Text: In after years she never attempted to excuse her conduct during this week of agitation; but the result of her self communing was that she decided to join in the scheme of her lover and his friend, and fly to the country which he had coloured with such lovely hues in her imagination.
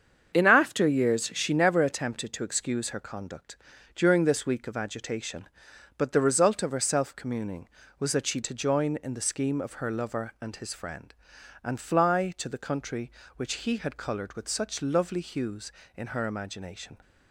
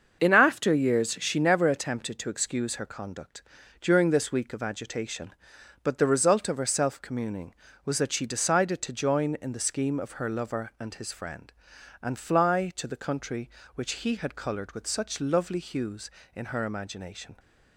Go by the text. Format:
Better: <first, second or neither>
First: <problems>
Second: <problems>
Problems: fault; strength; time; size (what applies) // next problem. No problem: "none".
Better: second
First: starts louder than the rest; until 1.3 s; 7 dB // pauses between "conduct" and "during"; at 3.5 s; 0.38 s long // skips "decided"; at 8.4 s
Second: starts louder than the rest; until 1.2 s; 6.5 dB // pauses between "conduct" and "during"; at 3.4 s; 0.38 s long